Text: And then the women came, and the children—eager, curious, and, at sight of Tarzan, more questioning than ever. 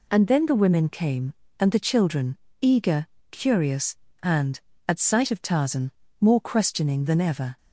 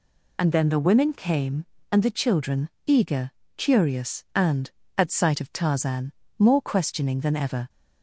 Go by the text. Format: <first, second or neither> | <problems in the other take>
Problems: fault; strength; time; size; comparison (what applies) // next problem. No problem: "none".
first | loses the start of "And"; at 0.3 s; 25 ms